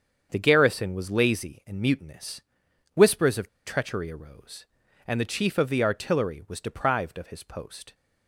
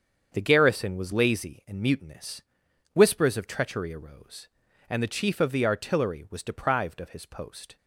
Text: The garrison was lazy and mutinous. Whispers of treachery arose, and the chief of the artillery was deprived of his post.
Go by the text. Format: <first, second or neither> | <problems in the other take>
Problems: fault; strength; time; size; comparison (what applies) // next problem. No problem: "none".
second | starts louder than the rest; strong; until 1.3 s; 7 dB; strong in the second // pauses between "of" and "treachery"; slight; at 3.4 s; 0.18 s long